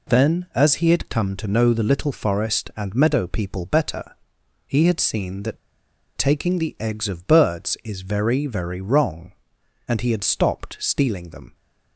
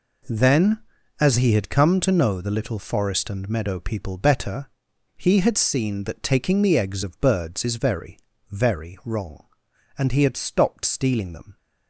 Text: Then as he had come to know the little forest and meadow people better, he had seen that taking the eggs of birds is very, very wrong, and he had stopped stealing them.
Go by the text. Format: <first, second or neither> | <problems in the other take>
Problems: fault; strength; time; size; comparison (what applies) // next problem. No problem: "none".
second | pauses between "that" and "taking"; noticeable; at 5.5 s; 0.58 s long